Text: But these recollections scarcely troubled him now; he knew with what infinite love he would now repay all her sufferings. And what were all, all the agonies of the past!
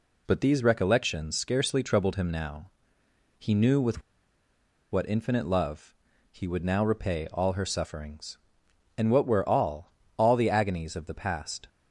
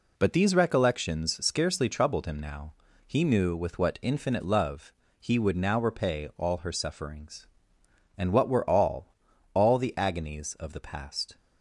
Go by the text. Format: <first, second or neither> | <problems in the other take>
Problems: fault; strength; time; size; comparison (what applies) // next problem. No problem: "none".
second | pauses between "with" and "what"; noticeable; at 4.0 s; 0.90 s long // pauses between "love" and "he"; slight; at 5.9 s; 0.36 s long; slight in the second